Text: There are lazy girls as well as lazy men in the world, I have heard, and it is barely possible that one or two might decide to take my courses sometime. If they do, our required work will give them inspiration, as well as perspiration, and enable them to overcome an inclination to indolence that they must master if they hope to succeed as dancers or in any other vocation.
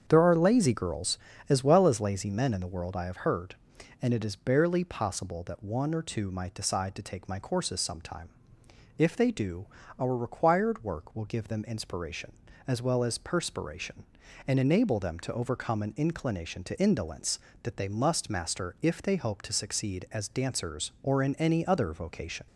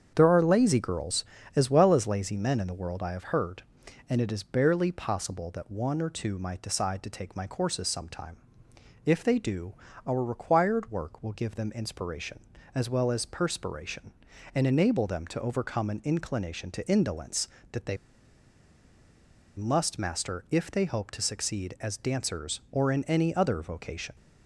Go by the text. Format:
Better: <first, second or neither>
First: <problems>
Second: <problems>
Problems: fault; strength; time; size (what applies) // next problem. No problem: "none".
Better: first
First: starts louder than the rest; strong; until 1.0 s; 7.5 dB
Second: starts louder than the rest; strong; until 1.1 s; 7.5 dB // pauses between "they" and "must"; strong; at 17.9 s; 1.6 s long